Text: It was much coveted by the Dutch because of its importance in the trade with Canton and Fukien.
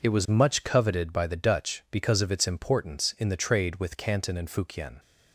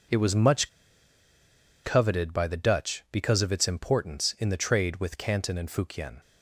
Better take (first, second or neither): first